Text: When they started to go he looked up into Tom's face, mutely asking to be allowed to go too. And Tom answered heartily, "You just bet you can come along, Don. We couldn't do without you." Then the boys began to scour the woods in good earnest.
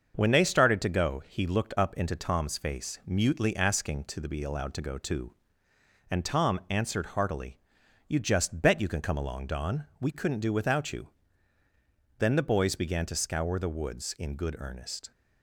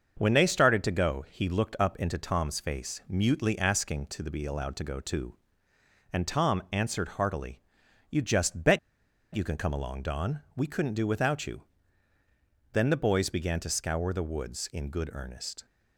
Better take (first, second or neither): first